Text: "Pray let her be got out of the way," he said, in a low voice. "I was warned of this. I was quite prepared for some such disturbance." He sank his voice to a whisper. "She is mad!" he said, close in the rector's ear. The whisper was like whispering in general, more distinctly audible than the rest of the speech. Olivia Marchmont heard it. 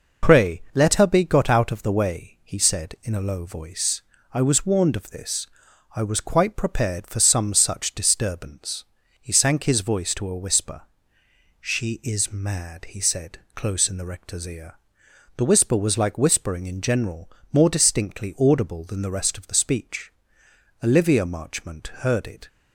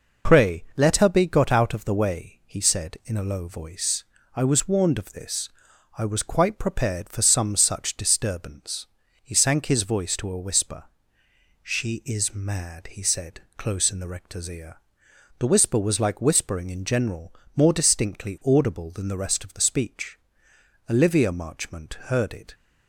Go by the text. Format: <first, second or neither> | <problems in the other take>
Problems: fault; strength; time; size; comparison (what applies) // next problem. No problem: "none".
neither | none